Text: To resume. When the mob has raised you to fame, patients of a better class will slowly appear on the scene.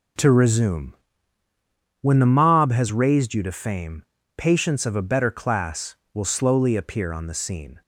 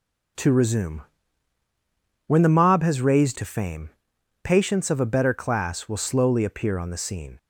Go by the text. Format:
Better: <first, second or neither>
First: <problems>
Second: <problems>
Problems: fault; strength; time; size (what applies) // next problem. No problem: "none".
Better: first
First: none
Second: skips "you"; at 3.3 s